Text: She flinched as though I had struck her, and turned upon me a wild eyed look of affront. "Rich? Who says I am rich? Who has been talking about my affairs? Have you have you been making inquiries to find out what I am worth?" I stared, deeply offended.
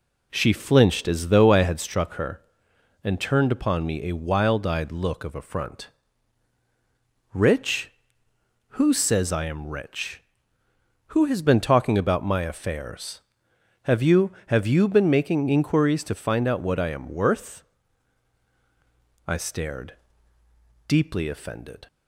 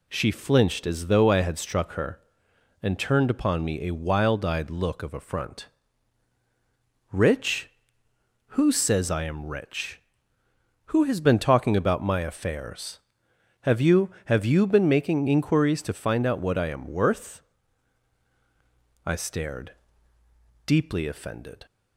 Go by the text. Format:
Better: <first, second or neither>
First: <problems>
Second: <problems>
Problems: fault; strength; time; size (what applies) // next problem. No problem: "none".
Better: second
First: starts louder than the rest; slight; until 1.9 s; 2 dB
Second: none